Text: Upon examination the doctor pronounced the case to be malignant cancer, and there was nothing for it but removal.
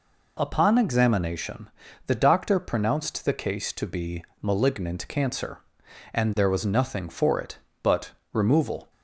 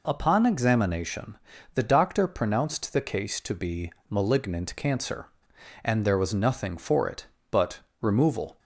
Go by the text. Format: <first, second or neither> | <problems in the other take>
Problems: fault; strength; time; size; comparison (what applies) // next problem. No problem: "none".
neither | pauses between "examination" and "the"; the same in both // pauses between "be" and "malignant"; slight; the same in both // pauses between "but" and "removal"; slight; the same in both